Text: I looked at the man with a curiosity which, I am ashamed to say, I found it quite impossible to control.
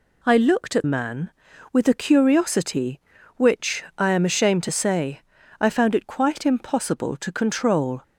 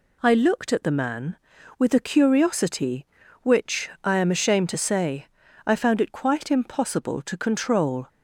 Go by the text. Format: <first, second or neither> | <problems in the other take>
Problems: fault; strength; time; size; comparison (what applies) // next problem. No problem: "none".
second | skips "the"; at 0.8 s